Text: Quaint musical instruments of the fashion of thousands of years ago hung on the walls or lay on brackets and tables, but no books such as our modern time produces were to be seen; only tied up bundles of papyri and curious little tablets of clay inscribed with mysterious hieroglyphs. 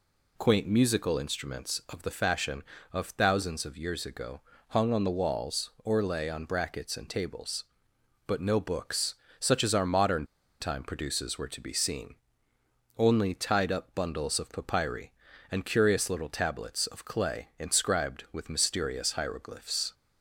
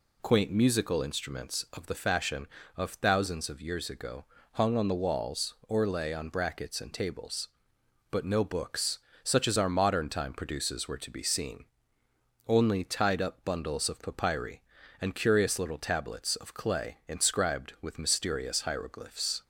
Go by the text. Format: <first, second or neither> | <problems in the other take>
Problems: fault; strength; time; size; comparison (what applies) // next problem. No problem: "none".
second | pauses between "ago" and "hung"; slight; at 4.3 s; 0.30 s long; slight in the second // pauses between "books" and "such"; slight; at 9.1 s; 0.24 s long; slight in the second // pauses between "modern" and "time"; slight; at 10.2 s; 0.34 s long